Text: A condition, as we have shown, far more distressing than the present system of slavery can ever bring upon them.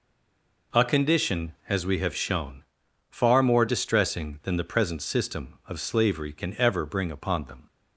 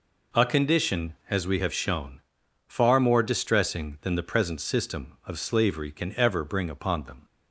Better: second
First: stays silent before the first word; slight; until 0.7 s; 0.7 s long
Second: none

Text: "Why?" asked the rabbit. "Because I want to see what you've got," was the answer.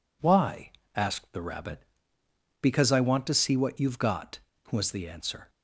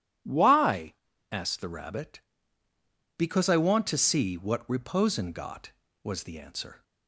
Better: first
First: none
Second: says "reposin" for "you've"; at 4.6 s

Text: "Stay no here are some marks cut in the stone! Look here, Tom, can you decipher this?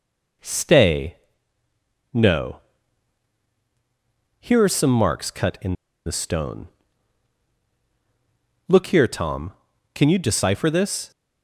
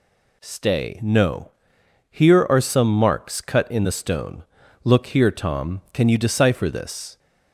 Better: second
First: pauses between "Stay" and "no"; noticeable; at 1.1 s; 0.98 s long // pauses between "no" and "here"; strong; at 2.5 s; 1.8 s long // pauses between "in" and "the"; slight; at 5.7 s; 0.31 s long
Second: pauses between "no" and "here"; noticeable; at 1.5 s; 0.58 s long

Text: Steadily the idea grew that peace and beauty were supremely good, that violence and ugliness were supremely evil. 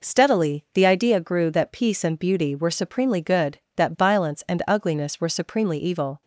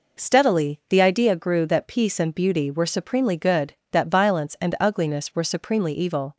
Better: neither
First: none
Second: none

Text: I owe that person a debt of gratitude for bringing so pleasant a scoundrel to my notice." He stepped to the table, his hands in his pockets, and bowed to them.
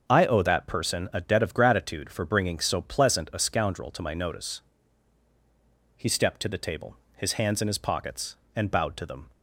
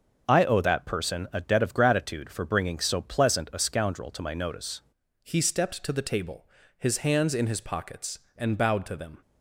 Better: first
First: starts louder than the rest; until 1.1 s; 6.5 dB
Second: starts louder than the rest; until 1.3 s; 6.5 dB // changes voice at "He"; from 5.2 s on; 3.9 s long

